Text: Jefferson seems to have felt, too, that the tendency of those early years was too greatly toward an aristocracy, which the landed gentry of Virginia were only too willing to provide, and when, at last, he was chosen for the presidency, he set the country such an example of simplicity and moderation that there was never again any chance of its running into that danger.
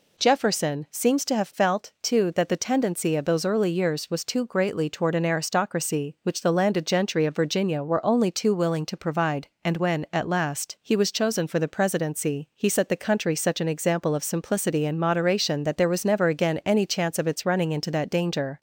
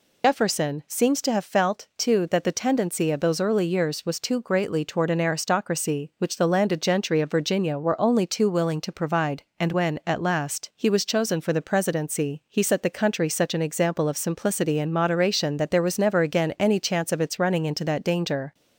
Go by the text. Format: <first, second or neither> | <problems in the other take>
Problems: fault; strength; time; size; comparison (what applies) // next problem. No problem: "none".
first | loses the start of "Jefferson"; at 0.2 s; 90 ms